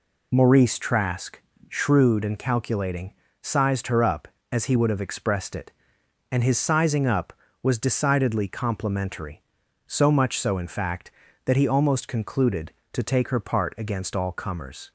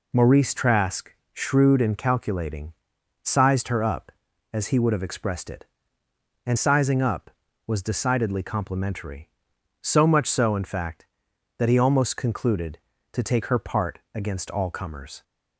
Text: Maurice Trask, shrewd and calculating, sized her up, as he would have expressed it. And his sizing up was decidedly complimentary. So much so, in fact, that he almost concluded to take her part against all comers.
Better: first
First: none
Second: skips "his"; at 6.5 s // pauses between "part" and "against"; slight; at 13.9 s; 0.16 s long

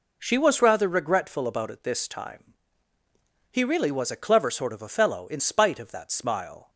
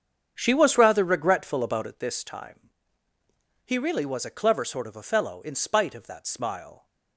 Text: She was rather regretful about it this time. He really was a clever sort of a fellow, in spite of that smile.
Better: first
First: none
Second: starts louder than the rest; strong; until 2.1 s; 7.5 dB

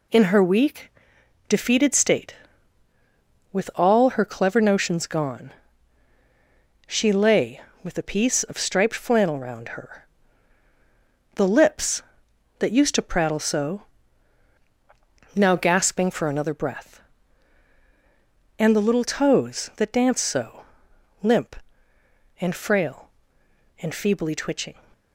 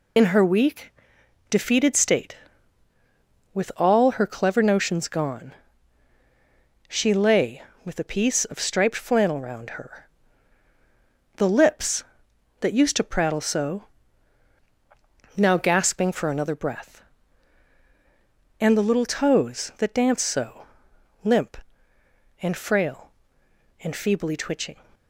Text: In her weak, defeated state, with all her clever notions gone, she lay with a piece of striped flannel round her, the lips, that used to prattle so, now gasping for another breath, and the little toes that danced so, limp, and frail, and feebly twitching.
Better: first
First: none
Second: loses the start of "In"; at 0.1 s; 45 ms

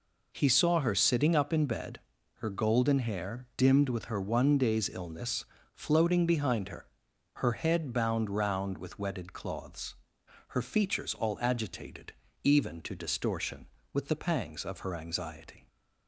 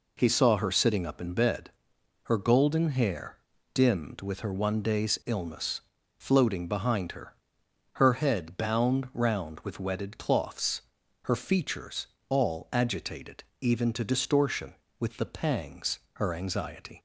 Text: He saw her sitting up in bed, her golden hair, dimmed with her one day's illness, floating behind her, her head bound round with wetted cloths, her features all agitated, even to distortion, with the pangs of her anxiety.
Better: first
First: none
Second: pauses between "features" and "all"; slight; at 12.0 s; 0.24 s long // skips "of"; at 16.0 s

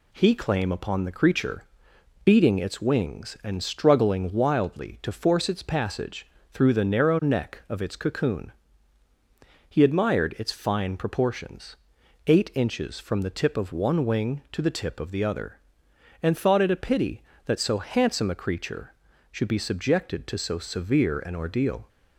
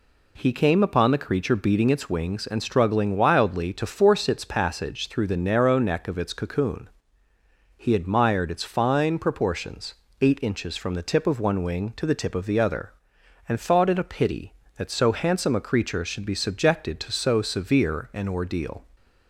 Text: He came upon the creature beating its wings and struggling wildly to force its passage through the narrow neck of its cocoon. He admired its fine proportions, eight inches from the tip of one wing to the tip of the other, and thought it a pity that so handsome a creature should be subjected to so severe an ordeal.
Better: second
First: says "claim" for "came"; at 0.3 s // pauses between "creature" and "beating"; noticeable; at 1.6 s; 0.60 s long // pauses between "passage" and "through"; slight; at 6.2 s; 0.24 s long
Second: none

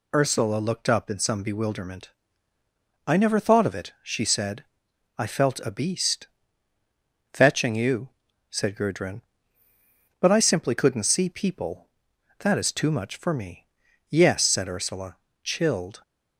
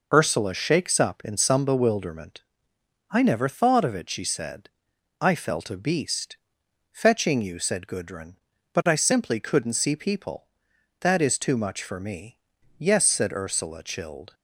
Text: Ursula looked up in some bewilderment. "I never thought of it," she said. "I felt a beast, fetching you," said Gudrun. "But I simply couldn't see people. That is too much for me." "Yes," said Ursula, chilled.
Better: first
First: none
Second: says "shakes" for "looked"; at 0.5 s

